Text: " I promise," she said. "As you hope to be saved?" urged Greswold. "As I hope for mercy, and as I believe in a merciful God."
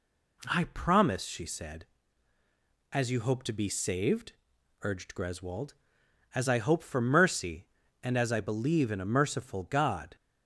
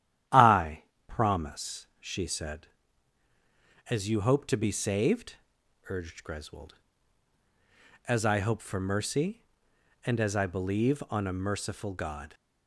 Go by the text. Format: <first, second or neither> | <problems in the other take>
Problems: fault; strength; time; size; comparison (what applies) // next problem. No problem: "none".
first | starts louder than the rest; strong; until 1.5 s; 11 dB // pauses between "I" and "promise"; slight; at 0.8 s; 0.24 s long // says "on" for "in"; at 11.0 s